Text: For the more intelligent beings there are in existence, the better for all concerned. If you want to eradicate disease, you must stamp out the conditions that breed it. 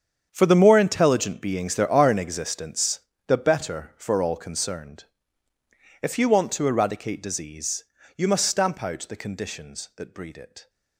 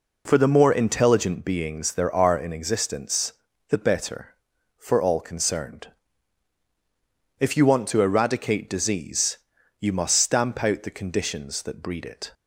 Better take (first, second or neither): second